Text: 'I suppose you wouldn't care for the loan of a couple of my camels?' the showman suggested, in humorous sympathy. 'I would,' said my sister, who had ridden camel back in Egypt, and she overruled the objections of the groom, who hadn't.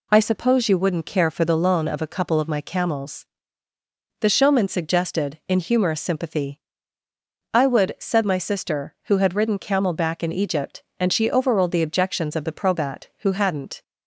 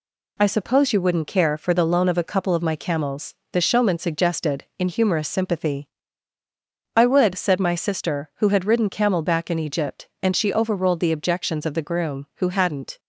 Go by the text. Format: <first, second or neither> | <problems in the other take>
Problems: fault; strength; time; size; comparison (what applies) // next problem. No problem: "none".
second | says "probat" for "groom"; at 12.5 s